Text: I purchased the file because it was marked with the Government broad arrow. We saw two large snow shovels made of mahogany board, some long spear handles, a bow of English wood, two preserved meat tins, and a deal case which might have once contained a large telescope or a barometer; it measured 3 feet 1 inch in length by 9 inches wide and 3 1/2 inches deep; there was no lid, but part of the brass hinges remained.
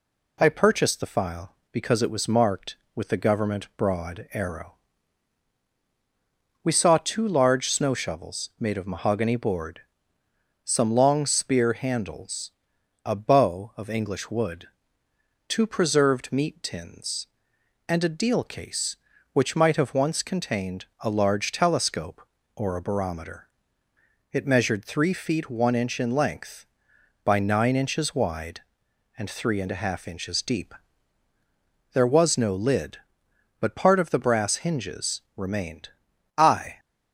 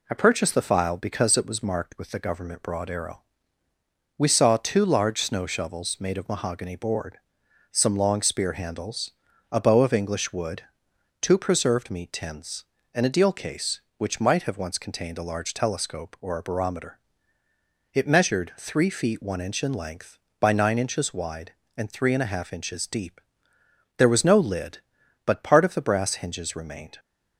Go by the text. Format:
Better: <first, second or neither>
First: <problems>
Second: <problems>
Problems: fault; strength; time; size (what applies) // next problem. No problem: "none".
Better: second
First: pauses between "contained" and "a"; slight; at 20.8 s; 0.16 s long // goes on to say "I"; slight; from 36.3 s on; 0.42 s long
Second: none